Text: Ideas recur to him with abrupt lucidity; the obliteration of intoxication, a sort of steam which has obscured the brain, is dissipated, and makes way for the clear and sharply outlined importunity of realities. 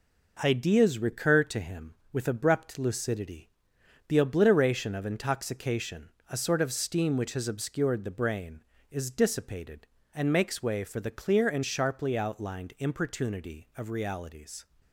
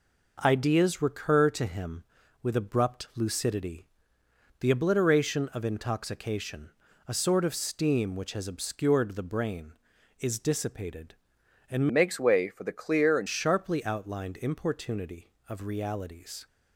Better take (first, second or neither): first